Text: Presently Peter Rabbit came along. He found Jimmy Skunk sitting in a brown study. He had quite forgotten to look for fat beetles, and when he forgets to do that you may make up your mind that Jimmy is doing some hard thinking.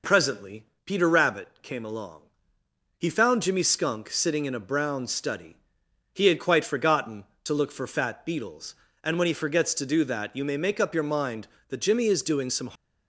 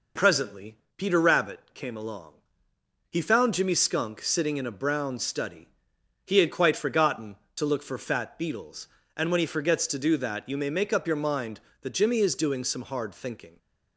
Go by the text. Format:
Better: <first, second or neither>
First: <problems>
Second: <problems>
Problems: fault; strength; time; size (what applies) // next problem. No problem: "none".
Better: second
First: pauses between "Presently" and "Peter"; slight; at 0.6 s; 0.18 s long // pauses between "Rabbit" and "came"; slight; at 1.4 s; 0.16 s long // stops before "hard thinking"; at 12.7 s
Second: pauses between "Presently" and "Peter"; slight; at 0.7 s; 0.18 s long // pauses between "Rabbit" and "came"; slight; at 1.5 s; 0.16 s long